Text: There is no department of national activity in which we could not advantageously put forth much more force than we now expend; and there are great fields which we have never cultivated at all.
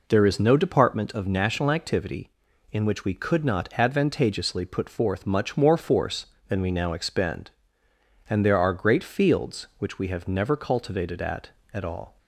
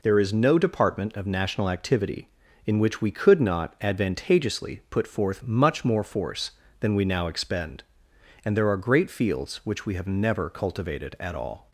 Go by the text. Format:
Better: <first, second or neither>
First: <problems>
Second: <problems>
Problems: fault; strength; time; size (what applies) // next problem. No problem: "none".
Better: second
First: says "at" twice; at 11.7 s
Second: none